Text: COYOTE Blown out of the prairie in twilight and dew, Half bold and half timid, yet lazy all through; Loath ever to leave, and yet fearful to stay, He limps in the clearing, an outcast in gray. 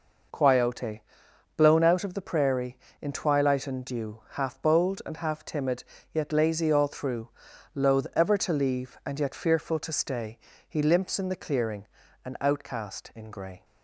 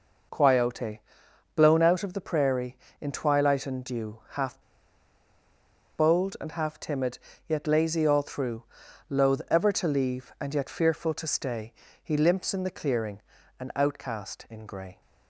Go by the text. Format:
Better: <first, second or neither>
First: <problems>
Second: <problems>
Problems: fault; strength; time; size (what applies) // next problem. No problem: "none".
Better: first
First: pauses between "COYOTE" and "Blown"; noticeable; at 1.0 s; 0.56 s long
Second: pauses between "COYOTE" and "Blown"; noticeable; at 0.9 s; 0.56 s long // pauses between "Half" and "bold"; strong; at 4.6 s; 1.3 s long